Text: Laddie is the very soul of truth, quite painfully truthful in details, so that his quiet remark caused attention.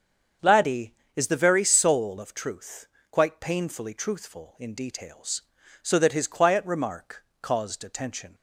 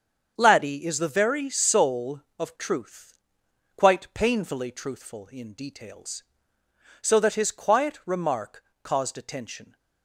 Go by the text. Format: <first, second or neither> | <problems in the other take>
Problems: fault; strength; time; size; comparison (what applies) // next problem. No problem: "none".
neither | starts louder than the rest; the same in both // pauses between "remark" and "caused"; slight; the same in both